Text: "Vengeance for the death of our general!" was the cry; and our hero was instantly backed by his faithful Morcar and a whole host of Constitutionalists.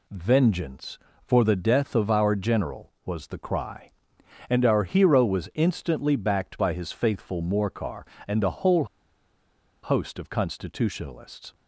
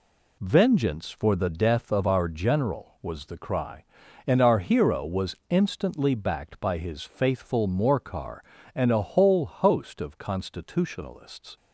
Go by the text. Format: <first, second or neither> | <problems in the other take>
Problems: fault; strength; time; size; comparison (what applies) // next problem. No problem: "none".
second | pauses between "whole" and "host"; at 8.8 s; 0.98 s long